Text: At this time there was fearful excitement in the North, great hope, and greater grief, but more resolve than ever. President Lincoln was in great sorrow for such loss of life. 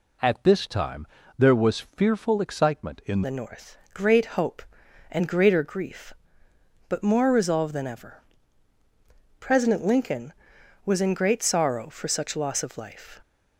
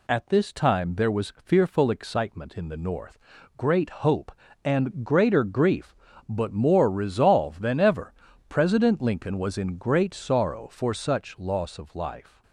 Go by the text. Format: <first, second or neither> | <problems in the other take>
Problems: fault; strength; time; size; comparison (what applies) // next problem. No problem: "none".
second | pauses between "time" and "there"; slight; at 1.0 s; 0.32 s long // changes voice at "the"; from 3.2 s on; 9.9 s long